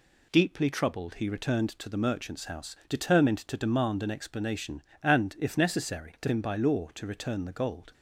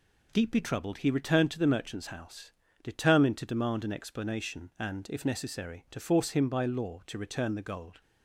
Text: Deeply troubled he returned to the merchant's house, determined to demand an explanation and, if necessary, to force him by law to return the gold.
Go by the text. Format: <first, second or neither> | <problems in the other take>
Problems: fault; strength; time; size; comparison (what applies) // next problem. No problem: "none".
second | skips "force"; at 6.2 s